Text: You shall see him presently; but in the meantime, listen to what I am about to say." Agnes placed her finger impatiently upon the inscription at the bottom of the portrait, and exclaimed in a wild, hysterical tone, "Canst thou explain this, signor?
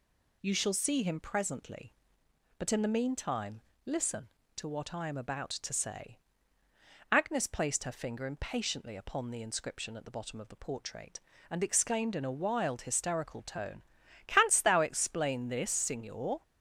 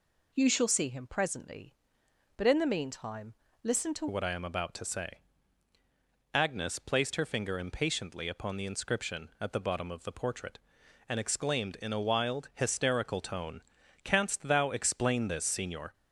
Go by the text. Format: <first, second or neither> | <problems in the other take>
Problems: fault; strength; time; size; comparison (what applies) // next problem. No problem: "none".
first | changes voice at "what"; from 4.1 s on; 11.8 s long